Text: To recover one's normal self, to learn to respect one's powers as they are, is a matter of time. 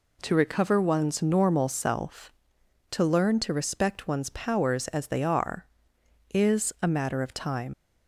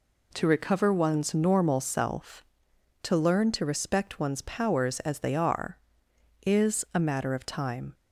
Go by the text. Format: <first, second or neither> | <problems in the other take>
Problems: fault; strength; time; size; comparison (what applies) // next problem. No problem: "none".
second | leaves "time" unfinished; at 7.7 s; 80 ms